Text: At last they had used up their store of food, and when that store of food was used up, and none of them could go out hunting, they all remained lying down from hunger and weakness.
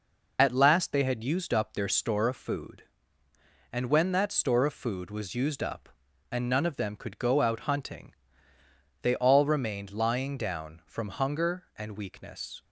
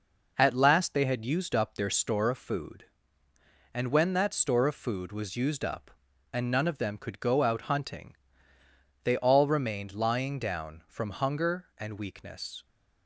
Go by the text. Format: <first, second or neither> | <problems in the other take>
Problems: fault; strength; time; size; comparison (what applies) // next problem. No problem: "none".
second | loses the start of "At"; at 0.3 s; 45 ms